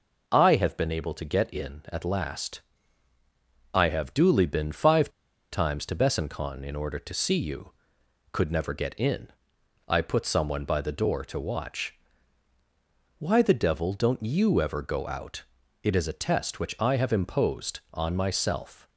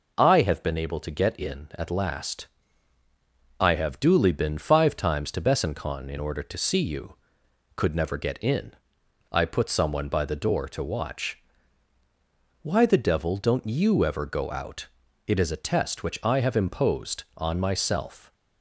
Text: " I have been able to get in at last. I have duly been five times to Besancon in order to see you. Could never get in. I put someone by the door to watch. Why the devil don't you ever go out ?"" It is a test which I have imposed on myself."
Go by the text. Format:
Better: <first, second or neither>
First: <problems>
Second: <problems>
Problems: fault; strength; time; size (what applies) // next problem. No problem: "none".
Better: second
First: pauses between "five" and "times"; at 5.0 s; 0.43 s long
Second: none